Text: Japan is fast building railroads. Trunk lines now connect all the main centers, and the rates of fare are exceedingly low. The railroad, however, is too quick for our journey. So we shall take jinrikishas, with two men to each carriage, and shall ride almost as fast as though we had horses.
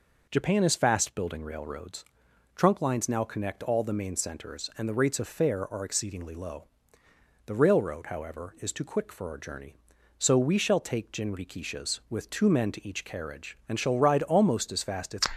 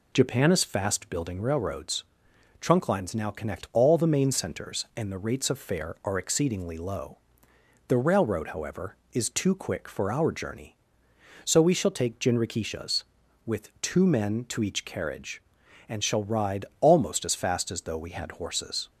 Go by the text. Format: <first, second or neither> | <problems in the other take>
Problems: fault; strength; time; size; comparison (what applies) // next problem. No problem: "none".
second | stops before "though we had horses"; at 15.3 s